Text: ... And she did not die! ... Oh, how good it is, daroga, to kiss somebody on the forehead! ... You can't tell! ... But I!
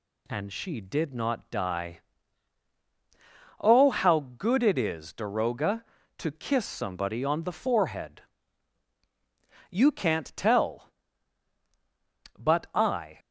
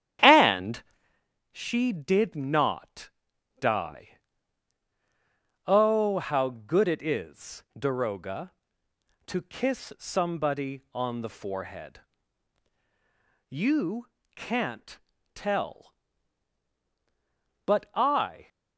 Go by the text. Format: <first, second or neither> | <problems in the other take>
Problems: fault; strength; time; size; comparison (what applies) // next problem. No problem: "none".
first | starts louder than the rest; strong; until 1.2 s; 10.5 dB // pauses between "And" and "she"; noticeable; at 0.8 s; 0.68 s long // pauses between "not" and "die"; noticeable; at 3.1 s; 0.48 s long // pauses between "You" and "can't"; slight; at 14.0 s; 0.28 s long // pauses between "can't" and "tell"; slight; at 14.9 s; 0.36 s long